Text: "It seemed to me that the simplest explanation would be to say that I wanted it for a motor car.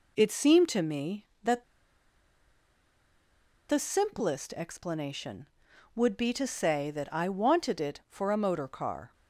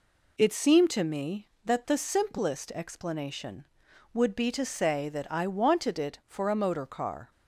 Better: second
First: pauses between "that" and "the"; strong; at 1.6 s; 2.0 s long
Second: none

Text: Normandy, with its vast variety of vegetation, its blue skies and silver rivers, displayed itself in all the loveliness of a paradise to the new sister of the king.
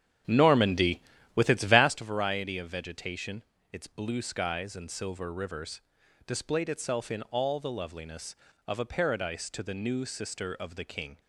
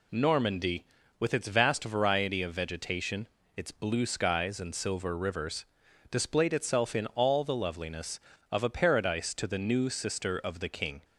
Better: second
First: starts louder than the rest; strong; until 2.0 s; 9.5 dB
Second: none

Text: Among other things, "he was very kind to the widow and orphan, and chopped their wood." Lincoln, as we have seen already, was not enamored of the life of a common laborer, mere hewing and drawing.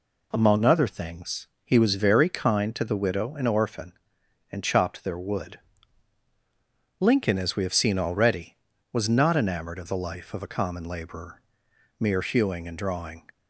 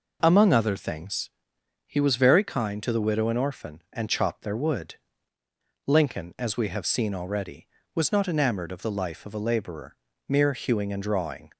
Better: first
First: none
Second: skips "common"; at 9.3 s

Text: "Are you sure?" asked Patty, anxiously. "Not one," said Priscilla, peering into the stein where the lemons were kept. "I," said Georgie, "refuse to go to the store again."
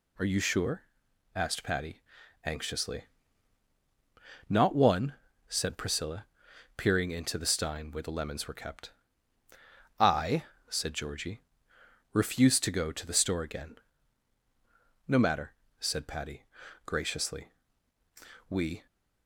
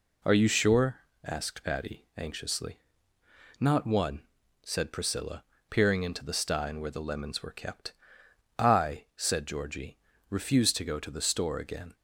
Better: second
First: goes on to say "No matter said Patty graciously we"; strong; from 15.0 s on; 3.8 s long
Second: none

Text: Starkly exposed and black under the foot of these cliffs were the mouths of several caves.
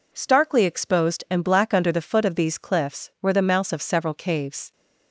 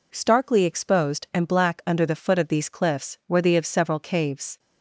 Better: first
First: none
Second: skips "mouths"; at 3.5 s

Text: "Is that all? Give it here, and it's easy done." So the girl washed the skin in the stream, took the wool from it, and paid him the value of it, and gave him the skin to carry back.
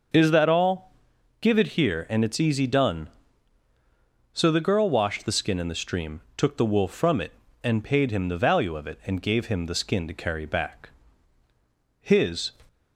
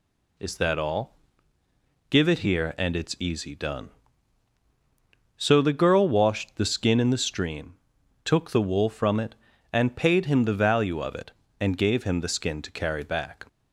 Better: second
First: starts louder than the rest; noticeable; until 1.6 s; 6 dB // goes on to say "His"; from 12.0 s on; 0.52 s long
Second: none

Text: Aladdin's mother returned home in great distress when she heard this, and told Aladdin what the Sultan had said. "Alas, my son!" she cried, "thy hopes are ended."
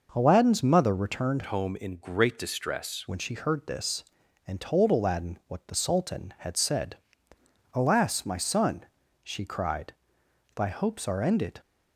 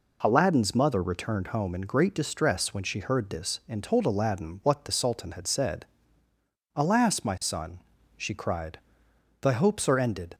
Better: second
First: changes voice from "home" to "distress"; from 1.4 to 3.0 s; 1.6 s long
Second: none

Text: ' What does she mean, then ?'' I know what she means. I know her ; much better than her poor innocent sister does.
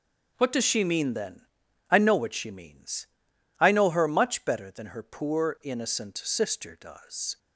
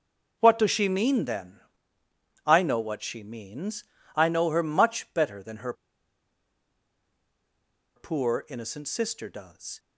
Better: first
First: none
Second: pauses between "her" and "poor"; strong; at 5.7 s; 2.2 s long

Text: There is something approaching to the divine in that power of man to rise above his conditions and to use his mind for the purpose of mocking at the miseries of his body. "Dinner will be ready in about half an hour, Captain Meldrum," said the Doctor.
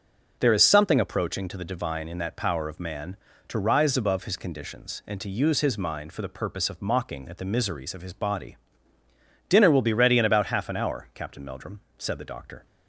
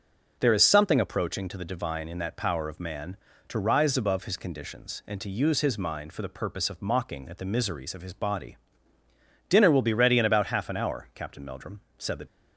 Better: first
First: none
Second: stops before "Doctor"; at 12.2 s

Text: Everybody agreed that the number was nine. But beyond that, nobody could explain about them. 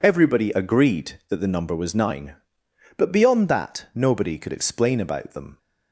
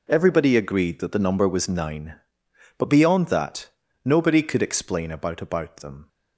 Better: first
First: none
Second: says "about" twice; at 5.4 s

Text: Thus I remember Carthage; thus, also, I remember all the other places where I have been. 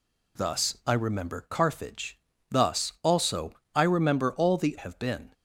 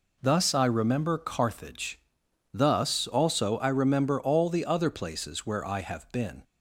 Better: second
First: skips "other places where I"; at 4.7 s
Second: none

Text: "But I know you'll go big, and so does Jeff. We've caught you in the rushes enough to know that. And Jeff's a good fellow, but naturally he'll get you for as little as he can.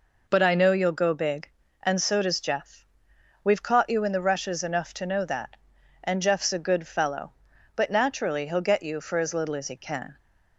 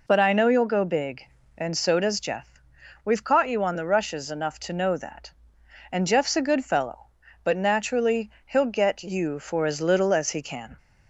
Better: first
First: none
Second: says "on" for "in"; at 3.6 s

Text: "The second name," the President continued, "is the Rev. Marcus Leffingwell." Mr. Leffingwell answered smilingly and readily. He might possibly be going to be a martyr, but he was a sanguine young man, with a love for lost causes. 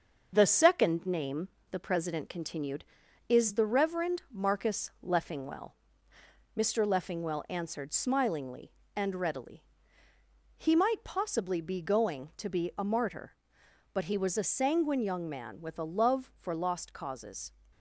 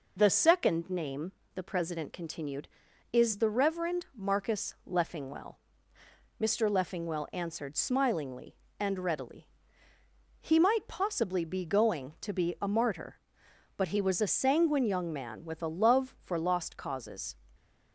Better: second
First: gets quieter; throughout; 4 dB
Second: none

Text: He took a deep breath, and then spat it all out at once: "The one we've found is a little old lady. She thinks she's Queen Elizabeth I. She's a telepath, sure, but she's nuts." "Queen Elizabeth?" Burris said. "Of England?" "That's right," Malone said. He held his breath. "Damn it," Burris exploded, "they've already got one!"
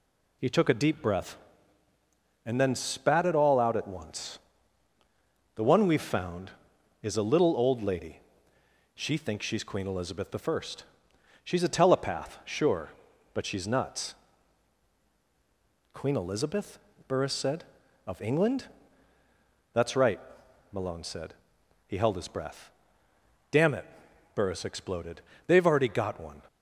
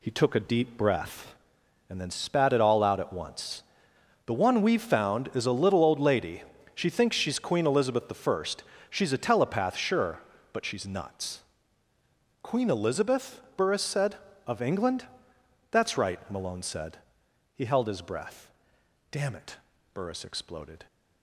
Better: first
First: none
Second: pauses between "Elizabeth" and "I"; slight; at 8.1 s; 0.16 s long // stops before "they've already got one"; at 20.8 s

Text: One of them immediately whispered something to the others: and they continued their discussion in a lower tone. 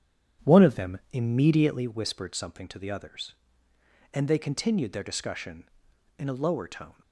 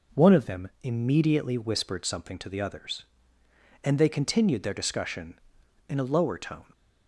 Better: second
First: starts louder than the rest; strong; until 1.9 s; 9 dB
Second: none

